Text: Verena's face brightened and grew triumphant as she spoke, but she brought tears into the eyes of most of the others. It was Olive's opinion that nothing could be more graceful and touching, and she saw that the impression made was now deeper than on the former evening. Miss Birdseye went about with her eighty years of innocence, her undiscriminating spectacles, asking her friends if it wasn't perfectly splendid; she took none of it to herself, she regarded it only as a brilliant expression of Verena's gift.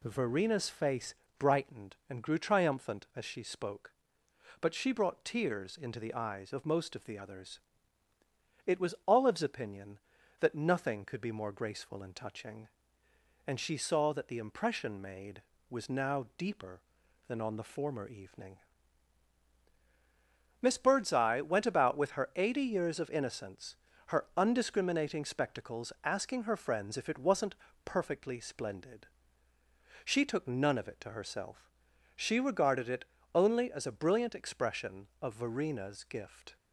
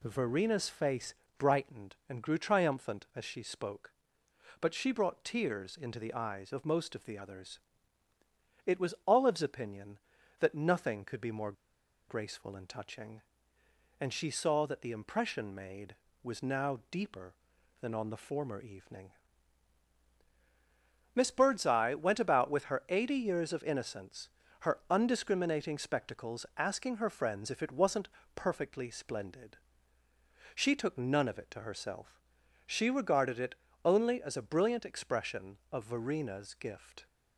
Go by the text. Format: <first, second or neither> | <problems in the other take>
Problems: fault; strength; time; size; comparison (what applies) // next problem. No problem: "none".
first | pauses between "face" and "brightened"; slight; at 1.1 s; 0.24 s long; slight in the first // pauses between "more" and "graceful"; noticeable; at 11.5 s; 0.56 s long // pauses between "wasn't" and "perfectly"; slight; at 28.0 s; 0.26 s long; slight in the first // pauses between "it" and "only"; slight; at 33.5 s; 0.28 s long; slight in the first